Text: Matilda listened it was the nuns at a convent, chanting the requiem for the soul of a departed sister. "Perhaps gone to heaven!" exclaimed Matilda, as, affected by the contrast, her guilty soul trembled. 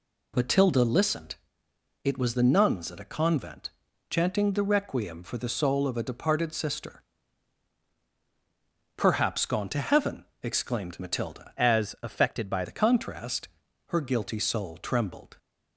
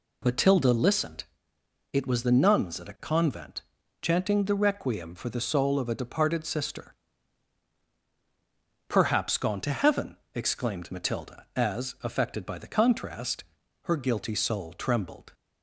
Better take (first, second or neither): second